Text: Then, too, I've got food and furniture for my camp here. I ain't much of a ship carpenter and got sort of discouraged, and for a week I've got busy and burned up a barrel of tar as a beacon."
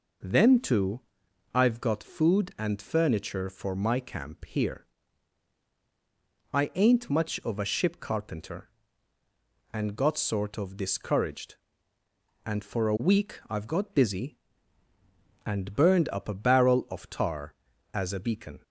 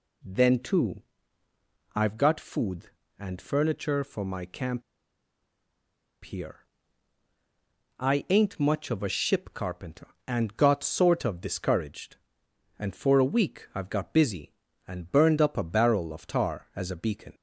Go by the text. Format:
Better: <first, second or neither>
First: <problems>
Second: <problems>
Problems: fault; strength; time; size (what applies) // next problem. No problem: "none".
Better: first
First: none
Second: pauses between "camp" and "here"; strong; at 4.8 s; 1.4 s long